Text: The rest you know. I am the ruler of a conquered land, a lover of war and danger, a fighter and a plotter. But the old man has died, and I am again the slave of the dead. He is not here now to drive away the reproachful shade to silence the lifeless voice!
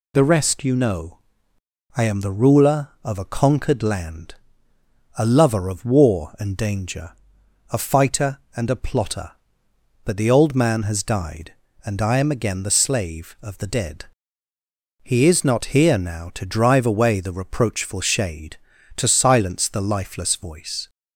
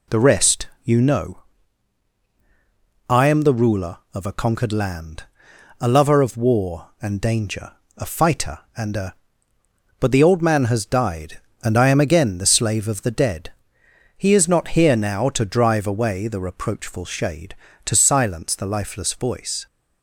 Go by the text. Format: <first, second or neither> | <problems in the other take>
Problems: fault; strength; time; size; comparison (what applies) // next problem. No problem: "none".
first | pauses between "rest" and "you"; slight; at 0.6 s; 0.16 s long // skips "plotter"; at 9.5 s